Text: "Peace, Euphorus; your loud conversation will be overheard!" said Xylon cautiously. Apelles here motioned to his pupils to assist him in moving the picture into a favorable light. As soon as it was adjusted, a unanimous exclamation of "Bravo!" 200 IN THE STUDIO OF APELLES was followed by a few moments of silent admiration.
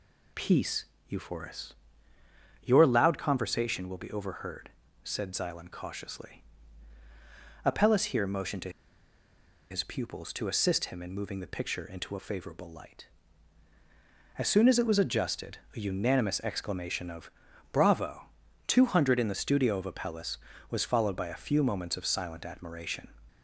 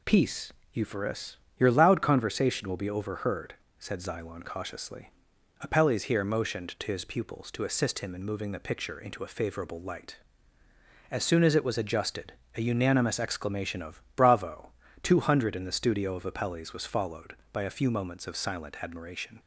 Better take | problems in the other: second | pauses between "to" and "his"; at 8.7 s; 0.99 s long // pauses between "of" and "Bravo"; at 17.2 s; 0.42 s long; slight in the second

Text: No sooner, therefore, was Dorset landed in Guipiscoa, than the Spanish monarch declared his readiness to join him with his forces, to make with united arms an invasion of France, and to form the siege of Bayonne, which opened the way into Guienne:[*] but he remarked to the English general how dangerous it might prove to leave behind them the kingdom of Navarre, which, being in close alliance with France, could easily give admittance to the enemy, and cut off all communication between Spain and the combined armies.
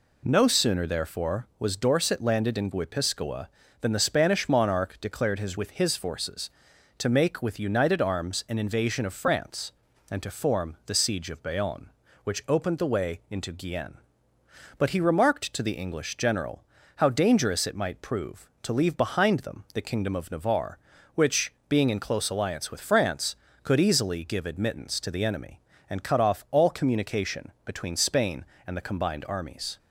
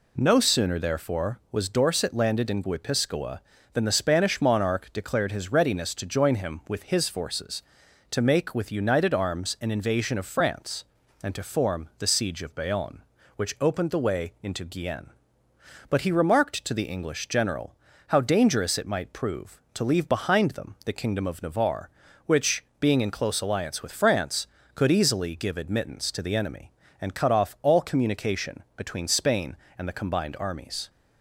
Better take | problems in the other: second | skips "readiness to join him"; at 5.5 s // pauses between "general" and "how"; slight; at 16.6 s; 0.32 s long; slight in the second

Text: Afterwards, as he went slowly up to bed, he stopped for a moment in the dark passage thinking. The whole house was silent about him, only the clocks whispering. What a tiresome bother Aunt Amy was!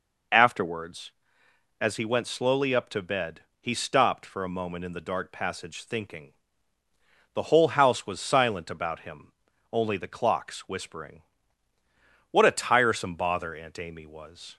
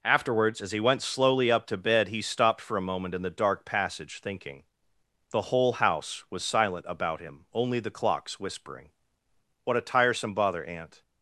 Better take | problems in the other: first | stops before "Amy was"; at 11.0 s

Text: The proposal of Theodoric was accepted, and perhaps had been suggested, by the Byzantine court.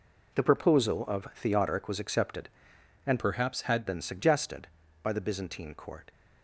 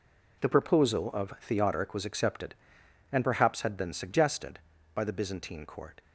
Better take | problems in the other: second | changes voice from "perhaps" to "had"; from 3.1 to 3.8 s; 0.7 s long

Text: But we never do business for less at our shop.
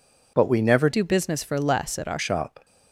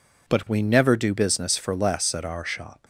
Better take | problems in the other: second | changes voice from "do" to "our"; from 0.9 to 2.1 s; 1.2 s long

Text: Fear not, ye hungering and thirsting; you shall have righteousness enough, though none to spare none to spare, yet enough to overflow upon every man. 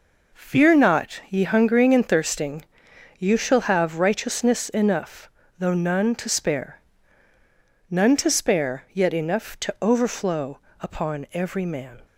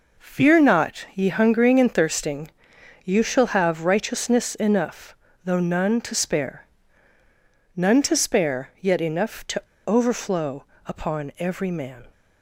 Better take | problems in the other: first | pauses between "spare" and "none"; at 6.6 s; 1.1 s long; also in the first // pauses between "to" and "overflow"; slight; at 9.6 s; 0.23 s long // pauses between "overflow" and "upon"; slight; at 10.6 s; 0.22 s long; slight in the first

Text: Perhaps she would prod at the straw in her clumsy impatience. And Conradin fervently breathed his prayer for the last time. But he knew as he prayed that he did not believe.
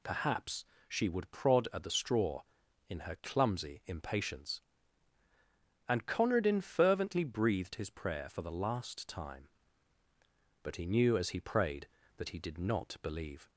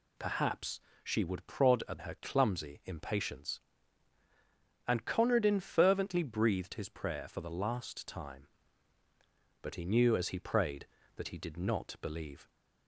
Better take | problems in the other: first | pauses between "Perhaps" and "she"; slight; at 0.8 s; 0.22 s long; slight in the first // skips "the straw in"; at 1.9 s

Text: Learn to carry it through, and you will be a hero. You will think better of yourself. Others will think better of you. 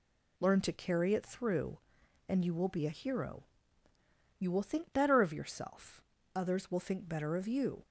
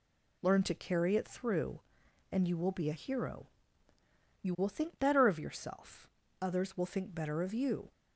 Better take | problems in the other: neither | none

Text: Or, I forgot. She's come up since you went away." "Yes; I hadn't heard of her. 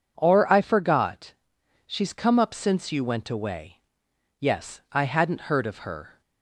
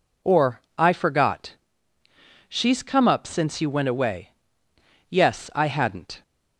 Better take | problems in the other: first | stops before "heard of her"; at 6.2 s

